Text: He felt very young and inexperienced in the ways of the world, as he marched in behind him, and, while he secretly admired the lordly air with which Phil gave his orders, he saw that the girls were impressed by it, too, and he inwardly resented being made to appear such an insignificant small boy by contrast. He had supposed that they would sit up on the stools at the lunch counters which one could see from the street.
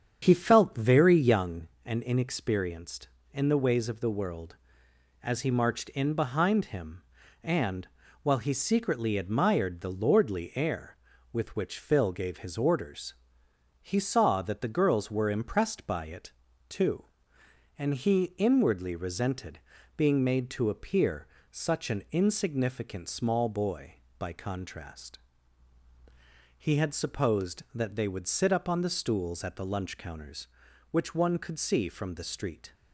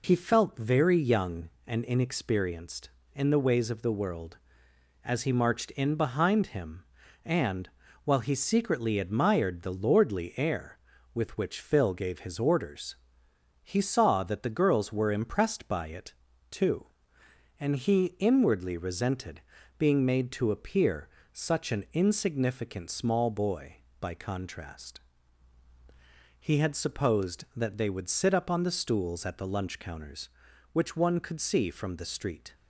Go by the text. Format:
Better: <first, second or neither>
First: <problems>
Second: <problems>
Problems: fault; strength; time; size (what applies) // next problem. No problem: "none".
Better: second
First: starts louder than the rest; strong; until 1.5 s; 8 dB // pauses between "resented" and "being"; at 19.5 s; 0.38 s long // pauses between "appear" and "such"; slight; at 21.2 s; 0.24 s long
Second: pauses between "resented" and "being"; at 19.4 s; 0.38 s long // pauses between "appear" and "such"; slight; at 21.0 s; 0.24 s long